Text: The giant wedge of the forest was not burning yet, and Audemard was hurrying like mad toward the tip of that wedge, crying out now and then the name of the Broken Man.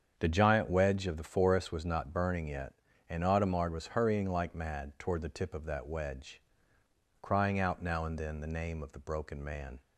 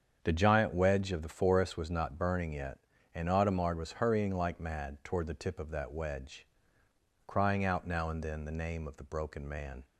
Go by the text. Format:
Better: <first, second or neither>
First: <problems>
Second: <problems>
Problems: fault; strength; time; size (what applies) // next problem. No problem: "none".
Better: neither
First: starts louder than the rest; strong; until 1.1 s; 7.5 dB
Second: starts louder than the rest; strong; until 1.2 s; 7.5 dB